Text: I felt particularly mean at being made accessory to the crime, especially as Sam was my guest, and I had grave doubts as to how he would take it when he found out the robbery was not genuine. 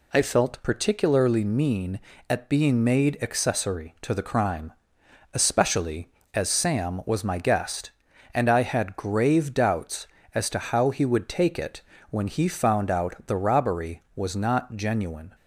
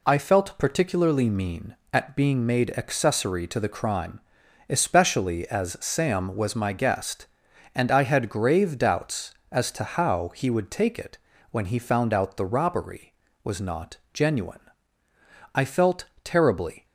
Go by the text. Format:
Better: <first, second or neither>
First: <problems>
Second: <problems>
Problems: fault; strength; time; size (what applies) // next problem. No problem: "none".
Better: first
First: pauses between "it" and "when"; slight; at 11.8 s; 0.30 s long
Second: pauses between "it" and "when"; slight; at 11.1 s; 0.32 s long // pauses between "not" and "genuine"; slight; at 13.9 s; 0.18 s long // goes on to say "I felt terribly"; noticeable; from 15.5 s on; 1.3 s long